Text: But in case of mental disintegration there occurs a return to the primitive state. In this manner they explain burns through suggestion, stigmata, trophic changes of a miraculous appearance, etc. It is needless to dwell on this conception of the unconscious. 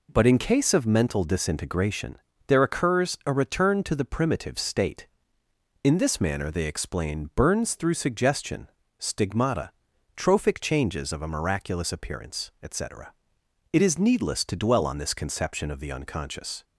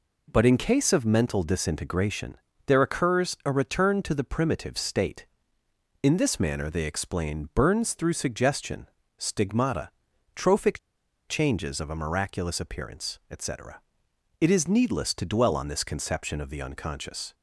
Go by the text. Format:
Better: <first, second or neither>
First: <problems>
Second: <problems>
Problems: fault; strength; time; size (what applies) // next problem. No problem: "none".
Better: first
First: pauses between "disintegration" and "there"; slight; at 2.1 s; 0.30 s long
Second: pauses between "disintegration" and "there"; slight; at 2.3 s; 0.30 s long // pauses between "trophic" and "changes"; noticeable; at 10.7 s; 0.49 s long